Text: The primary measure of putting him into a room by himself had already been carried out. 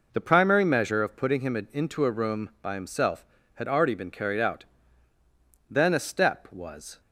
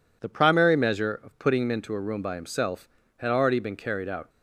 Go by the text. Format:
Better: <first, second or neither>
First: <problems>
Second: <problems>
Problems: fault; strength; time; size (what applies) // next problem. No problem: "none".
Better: second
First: pauses between "him" and "into"; slight; at 1.5 s; 0.16 s long // goes on to say "Then a step was"; from 5.6 s on; 1.3 s long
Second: none